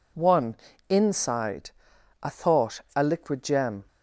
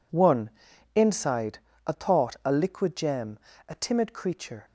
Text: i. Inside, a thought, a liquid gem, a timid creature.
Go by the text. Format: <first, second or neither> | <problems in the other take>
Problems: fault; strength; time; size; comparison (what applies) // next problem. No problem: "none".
second | stops before "a timid creature"; at 3.8 s